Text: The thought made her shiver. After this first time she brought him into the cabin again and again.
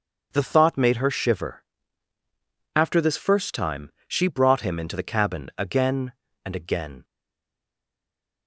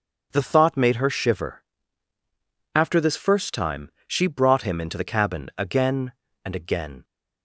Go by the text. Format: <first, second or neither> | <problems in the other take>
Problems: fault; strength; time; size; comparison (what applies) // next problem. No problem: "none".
second | starts louder than the rest; until 1.3 s; 6.5 dB; also in the second // pauses between "time" and "she"; slight; at 3.8 s; 0.18 s long; slight in the second // stays silent after the last word; noticeable; from 7.0 s on; 1.4 s long